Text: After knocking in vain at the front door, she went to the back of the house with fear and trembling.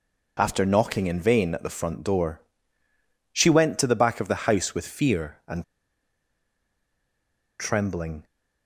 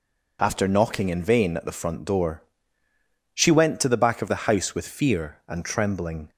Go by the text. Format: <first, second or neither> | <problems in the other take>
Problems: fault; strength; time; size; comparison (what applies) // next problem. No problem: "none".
second | pauses between "and" and "trembling"; strong; at 5.6 s; 1.9 s long